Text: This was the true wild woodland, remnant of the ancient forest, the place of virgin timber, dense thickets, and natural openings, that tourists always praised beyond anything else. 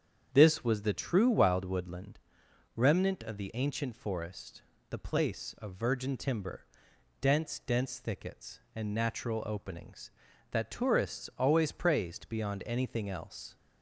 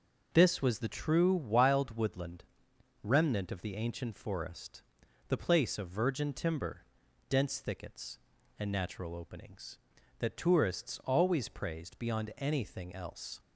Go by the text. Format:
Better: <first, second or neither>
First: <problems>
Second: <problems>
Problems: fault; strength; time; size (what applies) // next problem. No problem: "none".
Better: second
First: starts louder than the rest; strong; until 1.3 s; 8 dB // says "dense" twice; at 7.5 s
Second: none